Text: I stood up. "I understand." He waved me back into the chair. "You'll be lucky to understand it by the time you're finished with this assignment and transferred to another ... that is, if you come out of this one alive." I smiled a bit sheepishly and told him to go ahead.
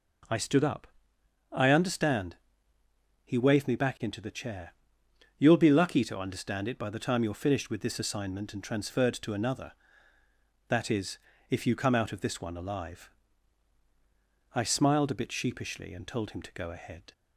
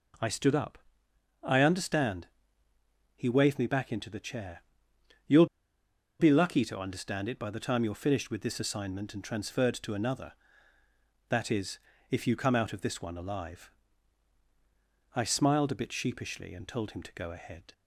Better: first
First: none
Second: pauses between "You'll" and "be"; noticeable; at 5.4 s; 0.74 s long

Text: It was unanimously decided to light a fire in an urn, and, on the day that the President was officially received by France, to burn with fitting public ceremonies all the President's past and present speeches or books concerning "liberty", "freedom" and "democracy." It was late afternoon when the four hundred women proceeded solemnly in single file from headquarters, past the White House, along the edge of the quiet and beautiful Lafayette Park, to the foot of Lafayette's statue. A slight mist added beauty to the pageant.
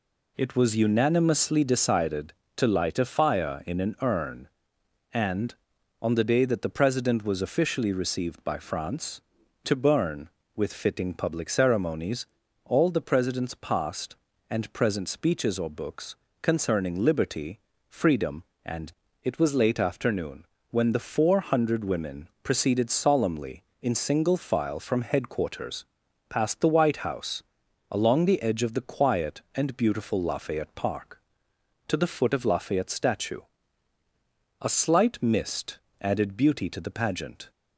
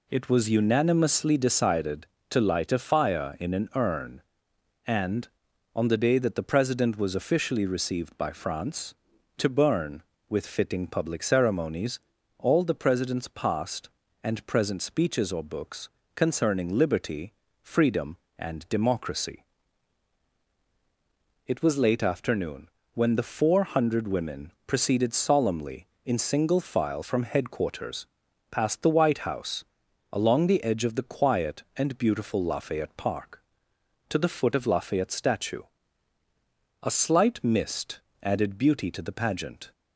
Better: second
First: pauses between "ceremonies" and "all"; at 12.2 s; 0.38 s long // pauses between "books" and "concerning"; slight; at 16.1 s; 0.26 s long // skips "democracy"; at 19.0 s // pauses between "afternoon" and "when"; slight; at 20.4 s; 0.24 s long // pauses between "mist" and "added"; slight; at 35.7 s; 0.22 s long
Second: pauses between "ceremonies" and "all"; at 11.9 s; 0.38 s long // pauses between "books" and "concerning"; slight; at 15.8 s; 0.26 s long // pauses between "afternoon" and "when"; slight; at 22.6 s; 0.24 s long // pauses between "mist" and "added"; slight; at 37.9 s; 0.22 s long

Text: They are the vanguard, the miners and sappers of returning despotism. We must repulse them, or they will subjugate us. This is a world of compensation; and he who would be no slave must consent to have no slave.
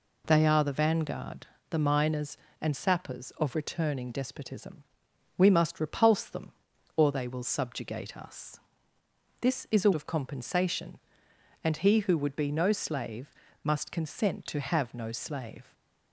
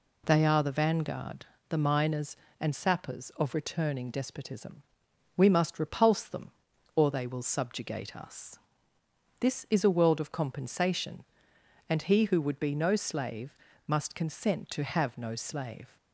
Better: second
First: skips "world"; at 9.9 s // pauses between "slave" and "must"; slight; at 13.3 s; 0.28 s long // stays silent after the last word; slight; from 15.6 s on; 0.5 s long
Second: pauses between "slave" and "must"; slight; at 13.5 s; 0.28 s long

